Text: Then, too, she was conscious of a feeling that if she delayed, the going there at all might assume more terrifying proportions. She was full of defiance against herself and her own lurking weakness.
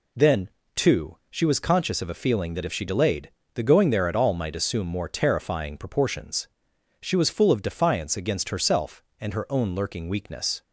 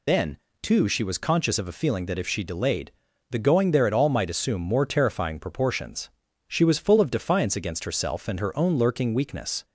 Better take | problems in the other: first | loses the start of "Then"; at 0.0 s; 50 ms

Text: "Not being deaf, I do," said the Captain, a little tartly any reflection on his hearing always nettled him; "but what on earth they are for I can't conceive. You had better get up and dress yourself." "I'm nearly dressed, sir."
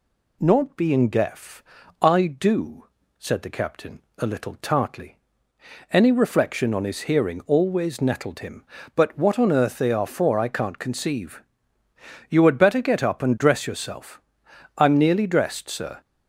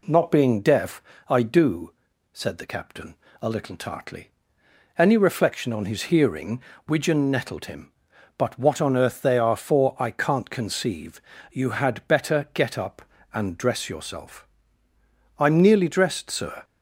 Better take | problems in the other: first | pauses between "tartly" and "any"; noticeable; at 4.2 s; 0.68 s long; noticeable in the first // says "widgeon" for "always"; at 6.8 s

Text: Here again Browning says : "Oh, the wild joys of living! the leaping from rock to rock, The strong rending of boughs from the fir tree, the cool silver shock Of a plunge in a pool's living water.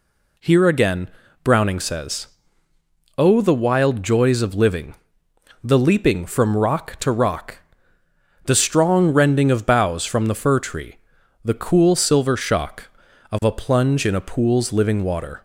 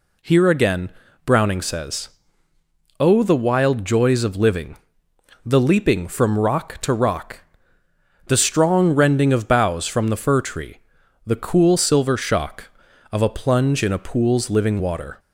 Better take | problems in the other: neither | pauses between "again" and "Browning"; slight; the same in both

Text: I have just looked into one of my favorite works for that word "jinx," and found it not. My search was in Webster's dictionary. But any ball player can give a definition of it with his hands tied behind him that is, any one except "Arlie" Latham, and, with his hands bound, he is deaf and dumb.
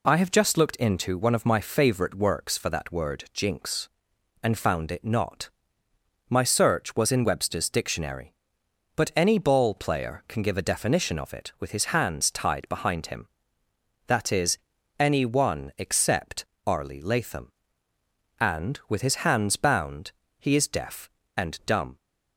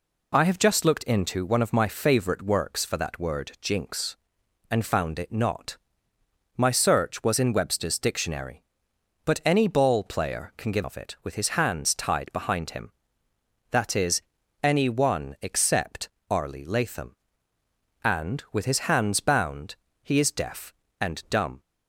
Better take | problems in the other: first | skips "a definition"; at 10.8 s // pauses between "except" and "Arlie"; slight; at 16.0 s; 0.22 s long; slight in the first

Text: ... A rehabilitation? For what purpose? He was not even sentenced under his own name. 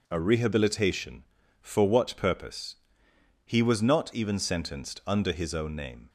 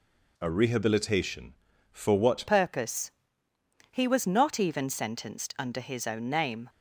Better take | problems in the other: first | changes voice at "purpose"; from 2.4 s on; 4.2 s long

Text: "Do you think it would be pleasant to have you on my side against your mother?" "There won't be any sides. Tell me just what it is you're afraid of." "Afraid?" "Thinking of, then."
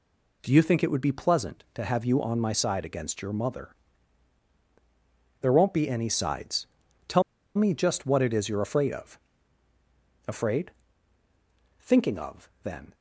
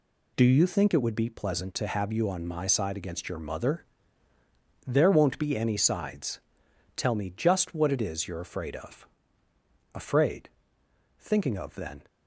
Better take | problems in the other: second | pauses between "Tell" and "me"; slight; at 7.2 s; 0.34 s long

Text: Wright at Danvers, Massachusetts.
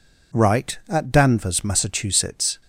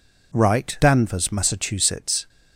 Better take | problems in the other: first | skips "at"; at 0.7 s

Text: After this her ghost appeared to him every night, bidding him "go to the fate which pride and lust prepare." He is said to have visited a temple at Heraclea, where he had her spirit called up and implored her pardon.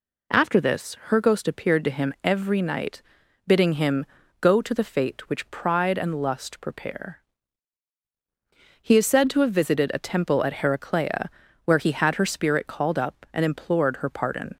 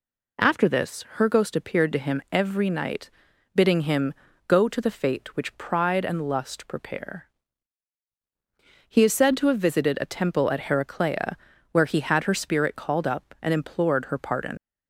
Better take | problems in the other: first | pauses between "him" and "go"; at 4.1 s; 0.36 s long; also in the first // leaves "pardon" unfinished; at 14.5 s; 75 ms

